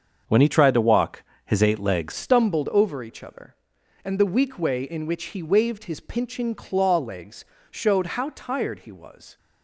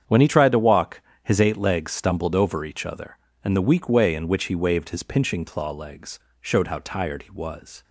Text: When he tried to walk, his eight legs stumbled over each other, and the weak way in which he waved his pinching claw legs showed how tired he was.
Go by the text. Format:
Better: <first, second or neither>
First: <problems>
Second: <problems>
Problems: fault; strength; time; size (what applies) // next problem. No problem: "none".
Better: second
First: starts louder than the rest; until 1.4 s; 7 dB // changes voice at "stumbled"; from 2.1 s on; 7.2 s long // pauses between "legs" and "showed"; slight; at 7.4 s; 0.26 s long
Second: starts louder than the rest; strong; until 1.2 s; 8 dB // pauses between "legs" and "showed"; slight; at 6.1 s; 0.22 s long